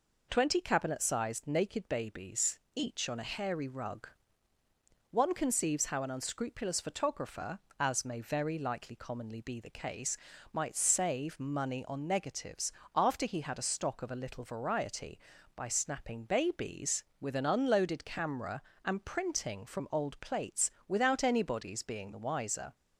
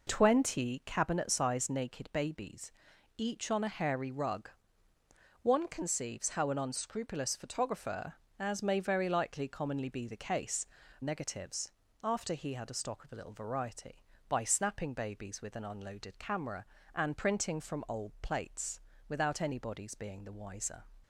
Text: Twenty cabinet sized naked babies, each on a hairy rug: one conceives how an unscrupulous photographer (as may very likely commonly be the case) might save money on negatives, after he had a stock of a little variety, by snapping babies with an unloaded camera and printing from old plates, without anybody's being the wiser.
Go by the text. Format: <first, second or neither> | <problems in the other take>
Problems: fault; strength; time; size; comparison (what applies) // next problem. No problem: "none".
first | skips "might save money on"; at 10.8 s